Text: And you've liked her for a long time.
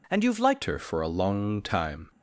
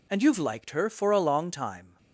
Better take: second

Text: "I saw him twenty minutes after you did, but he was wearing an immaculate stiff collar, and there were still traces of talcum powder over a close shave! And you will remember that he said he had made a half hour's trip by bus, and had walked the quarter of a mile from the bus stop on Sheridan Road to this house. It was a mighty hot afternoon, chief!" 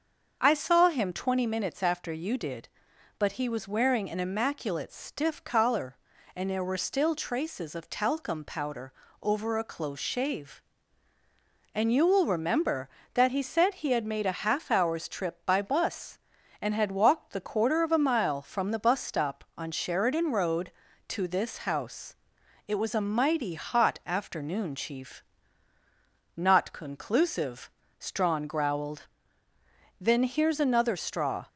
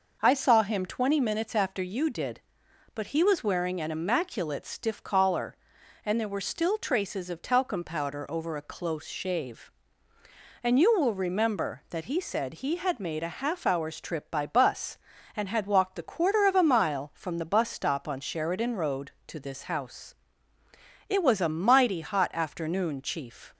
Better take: second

